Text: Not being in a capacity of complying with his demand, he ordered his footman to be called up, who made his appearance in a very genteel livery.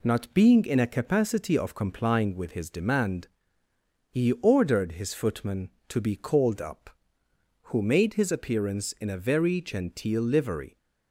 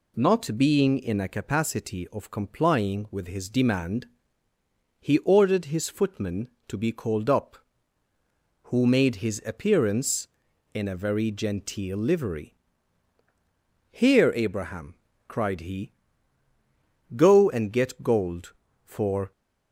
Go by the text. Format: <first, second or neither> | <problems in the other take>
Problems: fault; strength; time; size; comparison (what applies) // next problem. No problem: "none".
first | goes on to say "Here Abraham cried he go and get gold for"; strong; from 13.8 s on; 5.4 s long